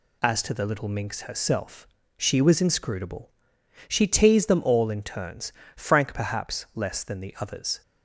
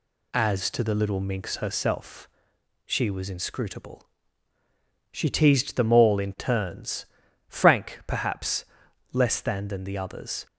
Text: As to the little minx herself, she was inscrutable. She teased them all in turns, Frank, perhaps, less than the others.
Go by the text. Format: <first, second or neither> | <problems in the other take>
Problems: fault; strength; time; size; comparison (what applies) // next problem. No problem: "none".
first | says "than" twice; at 9.6 s